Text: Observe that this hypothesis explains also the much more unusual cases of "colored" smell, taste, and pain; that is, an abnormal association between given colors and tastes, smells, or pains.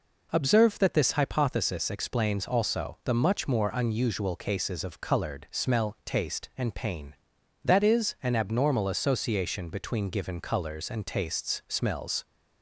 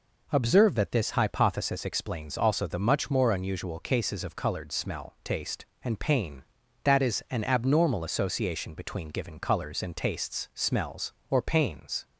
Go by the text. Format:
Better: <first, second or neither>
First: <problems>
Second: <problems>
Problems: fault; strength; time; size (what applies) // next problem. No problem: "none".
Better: second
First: stops before "or pains"; at 12.2 s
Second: none